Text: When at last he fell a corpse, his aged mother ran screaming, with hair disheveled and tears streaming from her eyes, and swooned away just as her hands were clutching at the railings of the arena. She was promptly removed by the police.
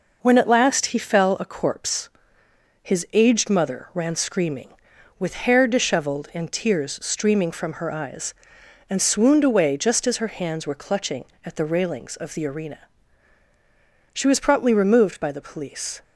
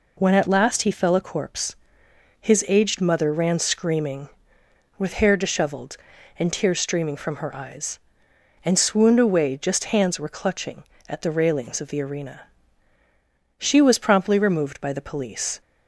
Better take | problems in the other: first | skips "as her"; at 9.9 s

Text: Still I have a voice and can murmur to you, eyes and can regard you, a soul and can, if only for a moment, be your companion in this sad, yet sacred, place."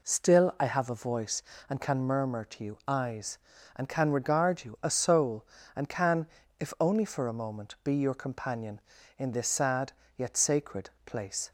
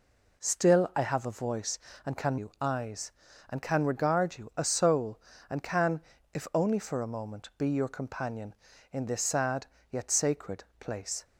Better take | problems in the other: first | skips "murmur to"; at 2.3 s

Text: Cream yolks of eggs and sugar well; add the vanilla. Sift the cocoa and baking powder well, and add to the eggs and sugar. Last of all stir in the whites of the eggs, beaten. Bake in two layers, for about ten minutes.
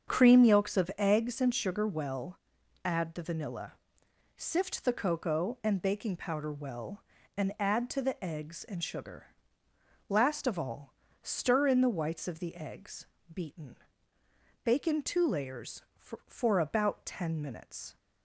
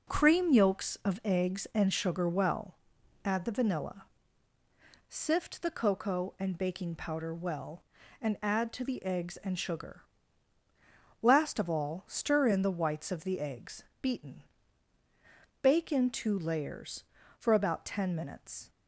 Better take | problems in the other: second | starts louder than the rest; strong; until 1.1 s; 7 dB // pauses between "all" and "stir"; slight; at 10.9 s; 0.26 s long // says "for" twice; at 16.2 s

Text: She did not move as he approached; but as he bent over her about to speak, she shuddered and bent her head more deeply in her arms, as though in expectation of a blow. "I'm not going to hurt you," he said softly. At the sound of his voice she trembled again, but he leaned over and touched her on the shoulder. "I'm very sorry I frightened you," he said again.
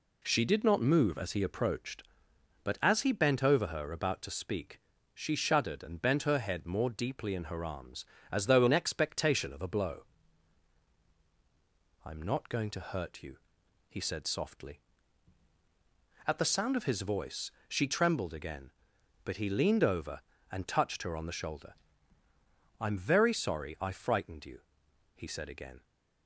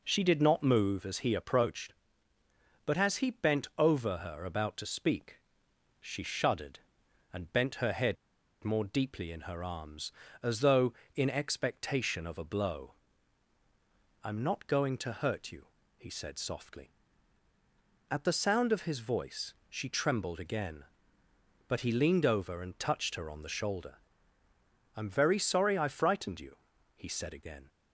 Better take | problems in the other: first | pauses between "head" and "more"; noticeable; at 8.1 s; 0.48 s long // pauses between "voice" and "she"; slight; at 19.5 s; 0.16 s long; slight in the first

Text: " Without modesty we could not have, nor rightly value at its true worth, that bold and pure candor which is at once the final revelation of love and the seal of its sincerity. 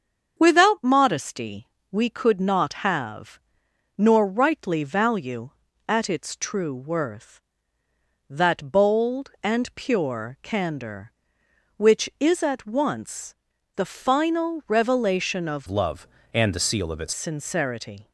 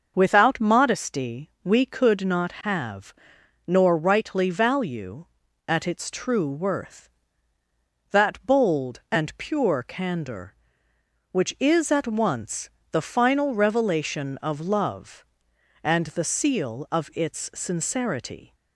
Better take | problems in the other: second | starts louder than the rest; until 1.3 s; 7 dB; noticeable in the second // pauses between "modesty" and "we"; slight; at 1.6 s; 0.24 s long // pauses between "once" and "the"; at 13.3 s; 0.40 s long; slight in the second // changes voice from "love" to "its"; from 15.6 to 17.1 s; 1.5 s long

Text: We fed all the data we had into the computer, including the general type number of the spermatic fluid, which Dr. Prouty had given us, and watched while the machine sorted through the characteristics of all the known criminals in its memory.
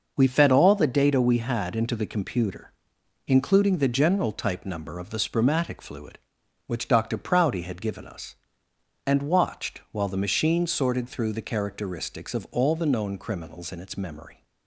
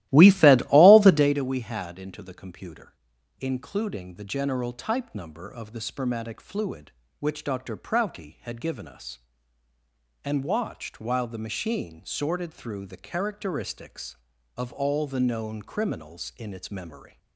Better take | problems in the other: first | starts louder than the rest; strong; until 1.4 s; 15.5 dB

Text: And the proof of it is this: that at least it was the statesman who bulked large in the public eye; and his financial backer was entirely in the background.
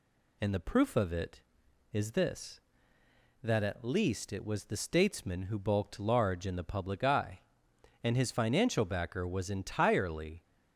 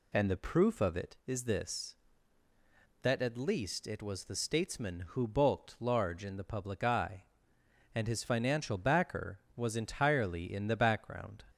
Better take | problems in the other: second | stops before "in the background"; at 10.4 s

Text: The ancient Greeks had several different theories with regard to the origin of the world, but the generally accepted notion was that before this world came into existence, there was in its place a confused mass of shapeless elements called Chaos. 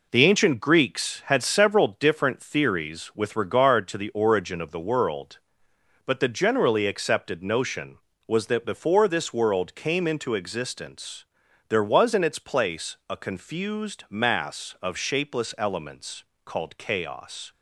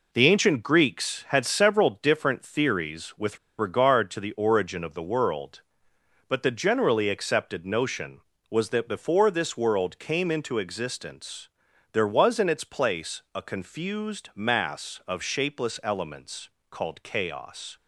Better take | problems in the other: first | pauses between "with" and "regard"; slight; at 3.3 s; 0.21 s long // pauses between "elements" and "called"; slight; at 16.4 s; 0.22 s long; slight in the first

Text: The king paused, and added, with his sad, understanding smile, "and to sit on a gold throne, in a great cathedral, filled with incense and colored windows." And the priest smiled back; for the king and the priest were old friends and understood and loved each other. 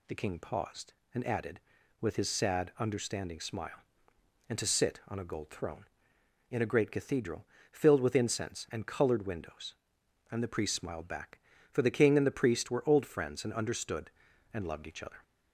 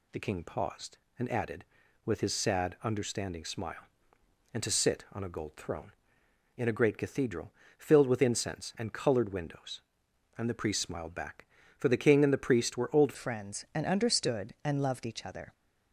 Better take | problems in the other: first | changes voice at "friends"; from 13.1 s on; 2.4 s long

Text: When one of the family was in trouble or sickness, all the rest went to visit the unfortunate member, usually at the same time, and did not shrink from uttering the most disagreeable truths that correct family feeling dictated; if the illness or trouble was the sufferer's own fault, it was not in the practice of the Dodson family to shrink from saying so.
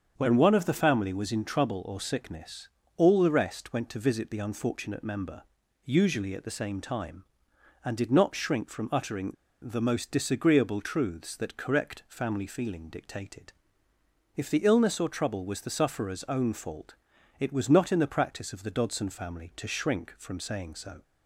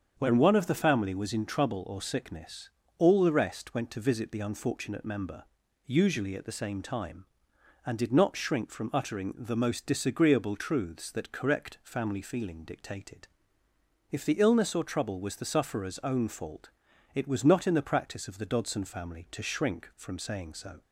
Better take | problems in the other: second | starts louder than the rest; strong; until 1.1 s; 7 dB; strong in the second // pauses between "uttering" and "the"; slight; at 9.3 s; 0.28 s long

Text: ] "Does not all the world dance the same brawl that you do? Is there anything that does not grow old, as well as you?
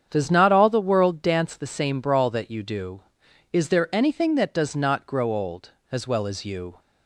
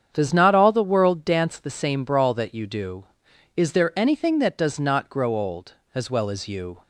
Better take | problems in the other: neither | starts louder than the rest; strong; the same in both

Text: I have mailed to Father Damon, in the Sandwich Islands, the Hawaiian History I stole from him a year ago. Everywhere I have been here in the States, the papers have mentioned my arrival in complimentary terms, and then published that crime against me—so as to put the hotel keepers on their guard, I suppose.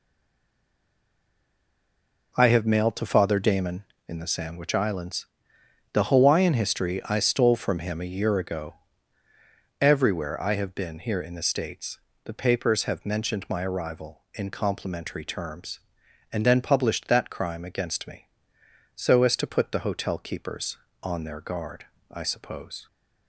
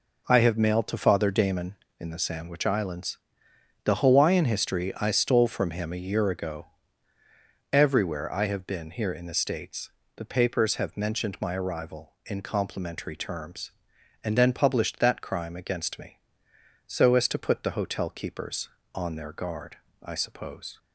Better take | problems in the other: second | stays silent before the first word; until 2.3 s; 2.3 s long

